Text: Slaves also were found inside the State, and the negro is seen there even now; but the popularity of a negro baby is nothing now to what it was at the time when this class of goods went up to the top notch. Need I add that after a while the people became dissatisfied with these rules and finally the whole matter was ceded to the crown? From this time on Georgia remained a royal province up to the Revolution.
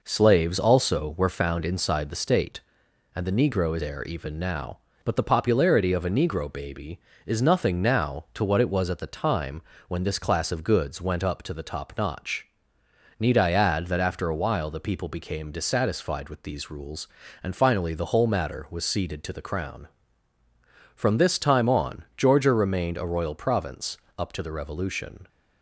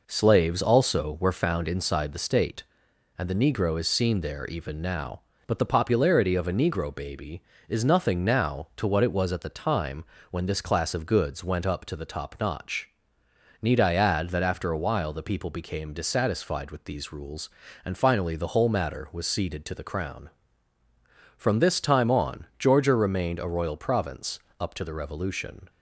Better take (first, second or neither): second